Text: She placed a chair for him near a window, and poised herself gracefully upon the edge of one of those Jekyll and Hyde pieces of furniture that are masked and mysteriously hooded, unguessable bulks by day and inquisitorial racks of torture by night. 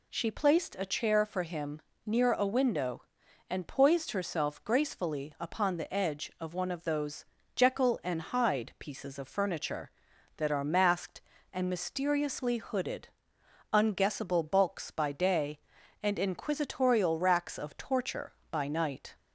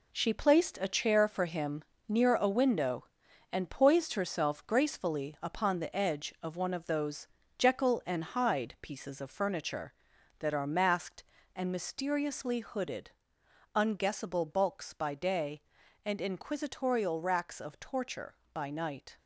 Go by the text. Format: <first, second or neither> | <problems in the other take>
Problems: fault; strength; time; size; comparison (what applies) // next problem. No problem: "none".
first | gets quieter; strong; throughout; 7.5 dB // pauses between "him" and "near"; slight; at 1.8 s; 0.26 s long; slight in the first // pauses between "those" and "Jekyll"; slight; at 7.2 s; 0.30 s long; slight in the first